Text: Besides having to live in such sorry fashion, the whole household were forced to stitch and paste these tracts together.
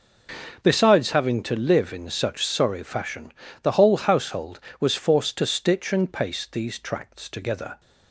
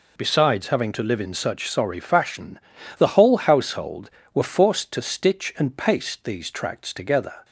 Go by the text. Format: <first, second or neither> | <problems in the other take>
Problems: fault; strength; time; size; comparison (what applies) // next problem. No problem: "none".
second | says "was" for "were"; at 4.7 s